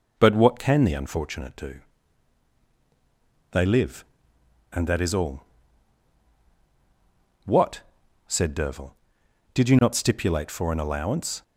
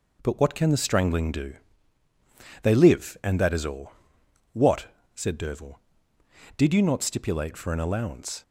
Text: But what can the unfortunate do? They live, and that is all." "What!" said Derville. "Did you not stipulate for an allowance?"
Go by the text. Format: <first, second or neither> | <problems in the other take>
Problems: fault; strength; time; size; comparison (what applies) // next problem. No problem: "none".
first | says "strangling" for "unfortunate"; at 0.7 s